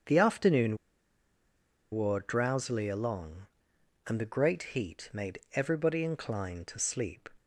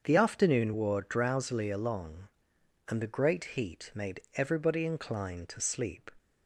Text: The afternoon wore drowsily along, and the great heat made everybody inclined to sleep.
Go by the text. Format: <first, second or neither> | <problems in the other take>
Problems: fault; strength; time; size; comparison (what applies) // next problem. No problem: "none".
second | starts louder than the rest; until 2.2 s; 7 dB; also in the second // pauses between "afternoon" and "wore"; at 0.7 s; 1.1 s long // pauses between "made" and "everybody"; slight; at 5.3 s; 0.16 s long; slight in the second